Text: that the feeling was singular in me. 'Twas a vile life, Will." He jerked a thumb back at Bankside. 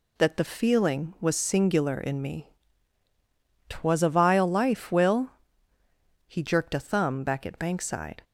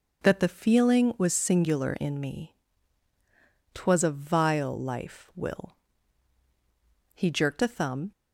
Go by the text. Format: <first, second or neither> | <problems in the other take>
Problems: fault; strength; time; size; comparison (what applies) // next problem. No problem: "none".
first | stops before "back at Bankside"; at 8.1 s